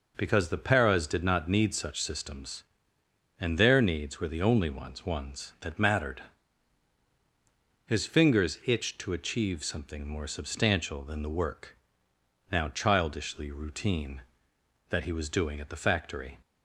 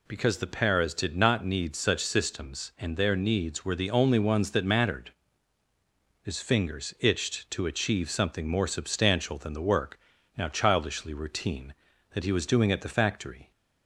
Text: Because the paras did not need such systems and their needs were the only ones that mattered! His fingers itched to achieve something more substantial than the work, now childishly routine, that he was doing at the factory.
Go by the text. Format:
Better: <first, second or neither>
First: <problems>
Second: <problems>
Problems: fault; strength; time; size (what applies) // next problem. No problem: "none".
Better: second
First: says "ones" twice; at 5.0 s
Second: none